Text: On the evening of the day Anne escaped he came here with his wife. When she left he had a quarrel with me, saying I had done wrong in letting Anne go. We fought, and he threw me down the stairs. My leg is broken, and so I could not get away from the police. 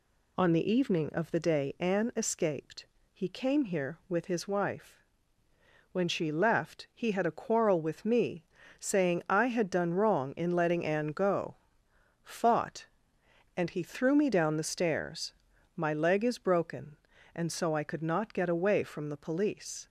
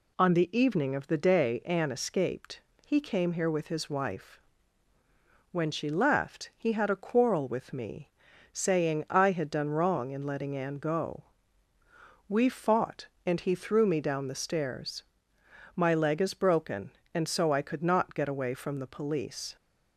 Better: second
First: pauses between "escaped" and "he"; slight; at 2.8 s; 0.26 s long // skips "We"; at 11.8 s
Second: pauses between "escaped" and "he"; slight; at 2.5 s; 0.24 s long

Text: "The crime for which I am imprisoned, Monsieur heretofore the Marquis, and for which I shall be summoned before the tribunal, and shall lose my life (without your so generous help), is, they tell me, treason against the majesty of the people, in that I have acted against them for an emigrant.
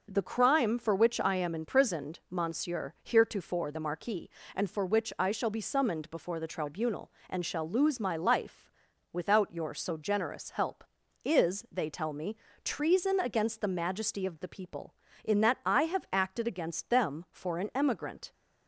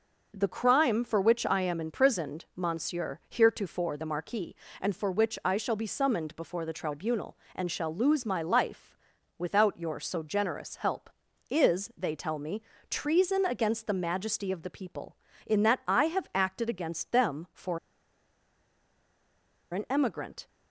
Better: first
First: none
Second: pauses between "for" and "an"; strong; at 17.7 s; 1.9 s long

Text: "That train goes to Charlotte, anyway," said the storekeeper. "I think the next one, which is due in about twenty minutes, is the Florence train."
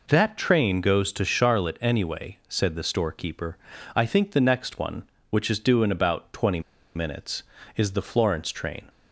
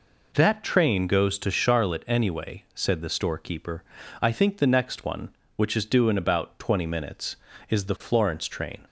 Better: second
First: pauses between "twenty" and "minutes"; slight; at 6.6 s; 0.35 s long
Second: none

